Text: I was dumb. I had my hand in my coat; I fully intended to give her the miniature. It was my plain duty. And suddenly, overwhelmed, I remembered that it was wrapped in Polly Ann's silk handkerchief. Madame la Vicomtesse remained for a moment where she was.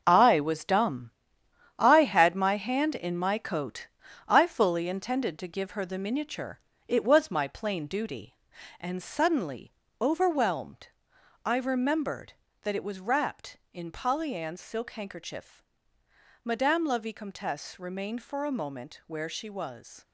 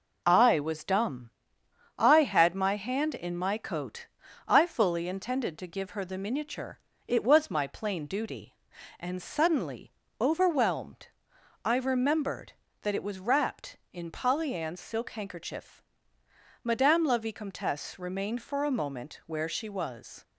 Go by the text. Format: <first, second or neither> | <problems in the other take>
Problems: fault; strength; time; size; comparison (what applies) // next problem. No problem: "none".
second | gets quieter; strong; throughout; 9.5 dB